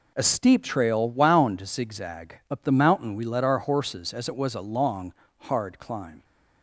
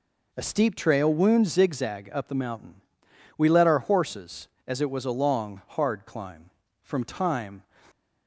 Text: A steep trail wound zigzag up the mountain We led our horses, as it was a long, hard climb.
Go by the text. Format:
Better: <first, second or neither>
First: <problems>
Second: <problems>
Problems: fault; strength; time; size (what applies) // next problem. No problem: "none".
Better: first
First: none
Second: pauses between "mountain" and "We"; noticeable; at 2.7 s; 0.60 s long // goes on to say "From time"; noticeable; from 6.8 s on; 0.82 s long